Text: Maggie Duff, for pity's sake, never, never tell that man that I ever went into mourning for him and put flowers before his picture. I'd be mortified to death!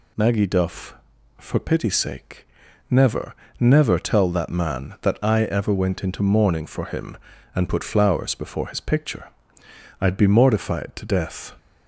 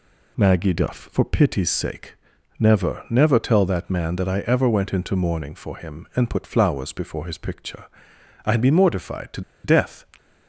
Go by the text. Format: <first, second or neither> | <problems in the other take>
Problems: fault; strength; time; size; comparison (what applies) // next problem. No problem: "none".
first | pauses between "to" and "death"; slight; at 9.4 s; 0.23 s long